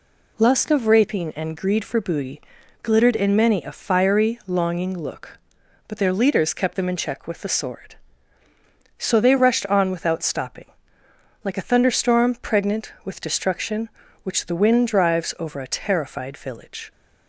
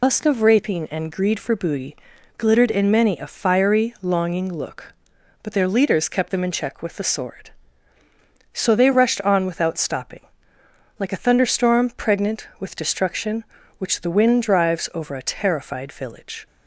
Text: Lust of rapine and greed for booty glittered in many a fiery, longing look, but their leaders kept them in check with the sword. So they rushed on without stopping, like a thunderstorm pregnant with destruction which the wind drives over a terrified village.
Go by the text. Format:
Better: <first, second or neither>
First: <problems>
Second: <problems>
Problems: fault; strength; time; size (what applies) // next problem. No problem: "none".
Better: first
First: pauses between "booty" and "glittered"; at 2.4 s; 0.42 s long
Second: loses the start of "Lust"; at 0.0 s; 110 ms // pauses between "booty" and "glittered"; at 1.9 s; 0.42 s long